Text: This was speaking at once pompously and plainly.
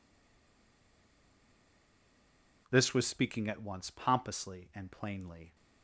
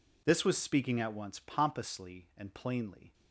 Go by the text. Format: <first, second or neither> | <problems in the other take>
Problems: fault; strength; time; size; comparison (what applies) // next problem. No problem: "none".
second | stays silent before the first word; strong; until 2.6 s; 2.6 s long